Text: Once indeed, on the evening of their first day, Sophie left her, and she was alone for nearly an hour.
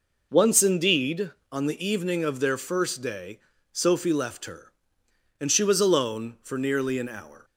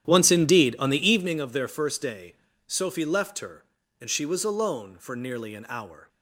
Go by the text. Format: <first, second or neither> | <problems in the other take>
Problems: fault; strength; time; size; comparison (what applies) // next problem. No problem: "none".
first | starts louder than the rest; strong; until 1.3 s; 10.5 dB